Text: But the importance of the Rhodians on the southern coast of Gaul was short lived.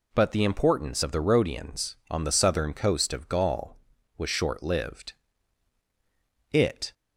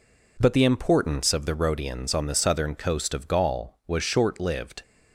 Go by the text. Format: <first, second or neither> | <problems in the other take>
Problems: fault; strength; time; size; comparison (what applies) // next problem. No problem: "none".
second | goes on to say "It"; slight; from 6.5 s on; 0.42 s long